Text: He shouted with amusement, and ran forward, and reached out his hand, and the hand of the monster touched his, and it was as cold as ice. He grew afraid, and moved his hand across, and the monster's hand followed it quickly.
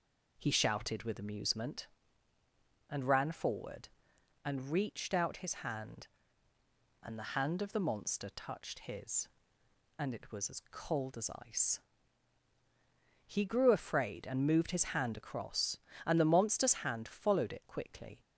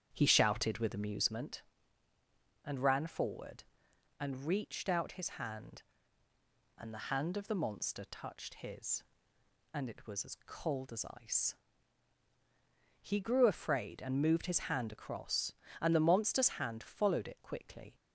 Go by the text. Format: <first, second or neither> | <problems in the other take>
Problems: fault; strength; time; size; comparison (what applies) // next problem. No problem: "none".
first | starts louder than the rest; strong; until 1.4 s; 8.5 dB // pauses between "as" and "ice"; slight; at 11.0 s; 0.18 s long; slight in the first